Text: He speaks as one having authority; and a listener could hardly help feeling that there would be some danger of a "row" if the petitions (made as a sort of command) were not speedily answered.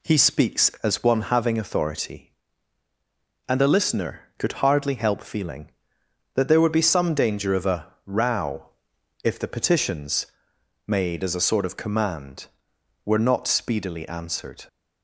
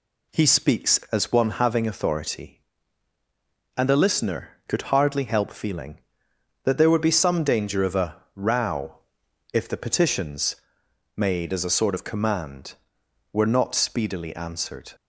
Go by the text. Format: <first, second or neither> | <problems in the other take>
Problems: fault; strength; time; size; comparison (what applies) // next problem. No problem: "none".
neither | pauses between "row" and "if"; noticeable; the same in both